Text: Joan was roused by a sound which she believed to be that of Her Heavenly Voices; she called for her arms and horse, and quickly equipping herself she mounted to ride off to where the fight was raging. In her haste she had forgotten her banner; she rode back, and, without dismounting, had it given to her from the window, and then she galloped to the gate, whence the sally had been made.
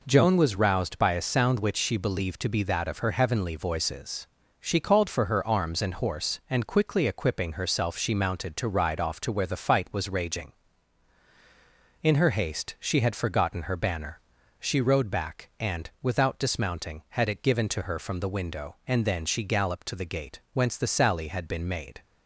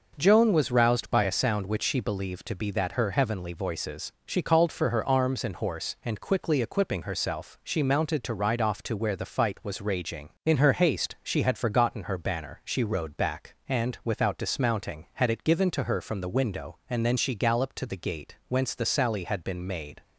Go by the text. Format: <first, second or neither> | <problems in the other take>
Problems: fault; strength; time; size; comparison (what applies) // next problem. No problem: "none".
first | skips "of"; at 2.9 s